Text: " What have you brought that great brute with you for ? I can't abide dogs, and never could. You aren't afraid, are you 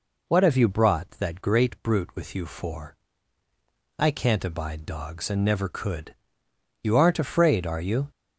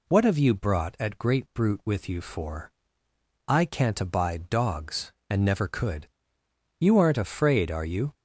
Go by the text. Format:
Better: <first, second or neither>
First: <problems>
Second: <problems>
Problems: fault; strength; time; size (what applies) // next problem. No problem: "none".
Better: first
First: none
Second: says "at" for "that"; at 1.0 s